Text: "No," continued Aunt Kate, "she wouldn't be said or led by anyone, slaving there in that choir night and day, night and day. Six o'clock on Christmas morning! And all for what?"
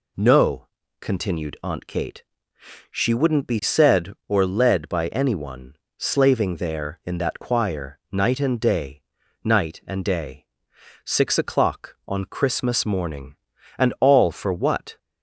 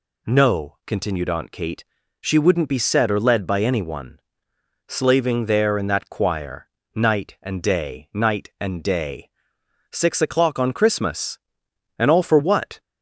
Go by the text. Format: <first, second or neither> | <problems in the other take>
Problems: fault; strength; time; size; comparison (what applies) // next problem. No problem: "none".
first | pauses between "choir" and "night"; slight; at 6.6 s; 0.26 s long // skips "morning"; at 11.6 s